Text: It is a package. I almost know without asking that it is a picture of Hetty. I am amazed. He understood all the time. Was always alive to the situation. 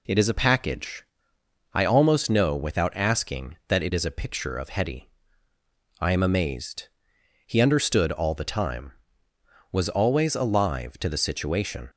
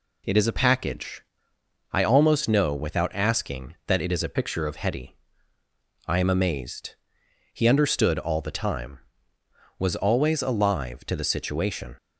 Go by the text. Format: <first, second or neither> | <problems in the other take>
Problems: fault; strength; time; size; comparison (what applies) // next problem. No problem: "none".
first | changes voice from "picture" to "of"; from 4.3 to 4.7 s; 0.4 s long